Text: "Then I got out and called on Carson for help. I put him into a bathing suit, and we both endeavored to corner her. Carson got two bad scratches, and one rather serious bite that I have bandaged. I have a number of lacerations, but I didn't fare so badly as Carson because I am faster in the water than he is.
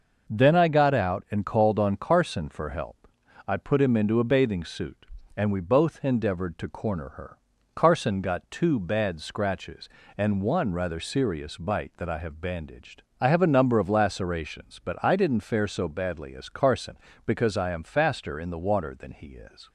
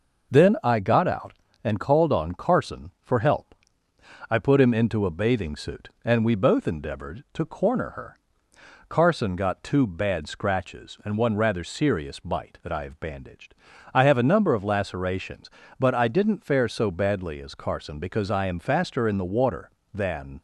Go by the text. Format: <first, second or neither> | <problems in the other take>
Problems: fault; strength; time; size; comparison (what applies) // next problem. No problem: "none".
first | stops before "he is"; at 20.3 s